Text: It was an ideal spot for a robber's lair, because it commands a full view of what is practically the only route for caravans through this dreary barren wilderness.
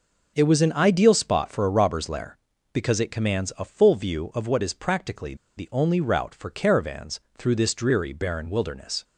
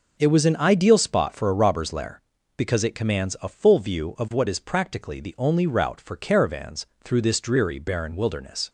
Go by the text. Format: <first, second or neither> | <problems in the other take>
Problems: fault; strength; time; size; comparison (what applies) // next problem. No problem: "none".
second | pauses between "practically" and "the"; slight; at 5.3 s; 0.21 s long // pauses between "caravans" and "through"; slight; at 7.1 s; 0.20 s long; slight in the second